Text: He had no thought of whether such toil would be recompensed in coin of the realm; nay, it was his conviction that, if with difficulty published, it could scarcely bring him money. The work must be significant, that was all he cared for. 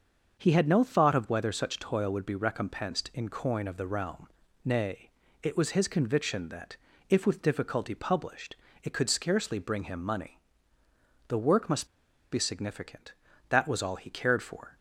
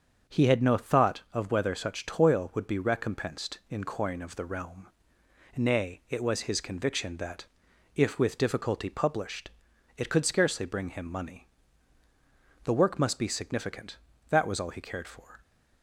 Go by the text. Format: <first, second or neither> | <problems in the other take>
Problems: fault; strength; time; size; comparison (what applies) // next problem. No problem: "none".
second | starts louder than the rest; until 1.4 s; 6.5 dB; also in the second // pauses between "must" and "be"; at 11.8 s; 0.44 s long